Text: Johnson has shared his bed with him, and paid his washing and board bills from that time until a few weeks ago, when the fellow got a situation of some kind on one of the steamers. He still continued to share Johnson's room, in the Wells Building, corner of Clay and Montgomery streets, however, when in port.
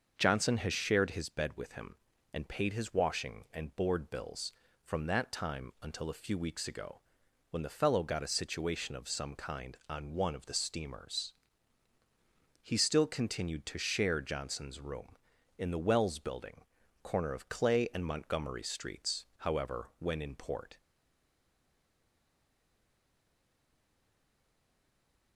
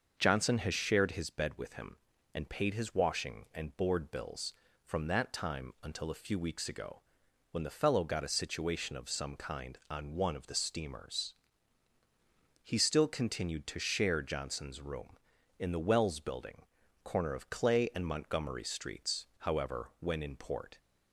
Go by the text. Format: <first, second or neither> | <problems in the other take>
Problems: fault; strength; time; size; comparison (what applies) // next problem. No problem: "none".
second | starts louder than the rest; until 1.1 s; 6.5 dB; also in the second // stays silent after the last word; strong; from 20.7 s on; 4.6 s long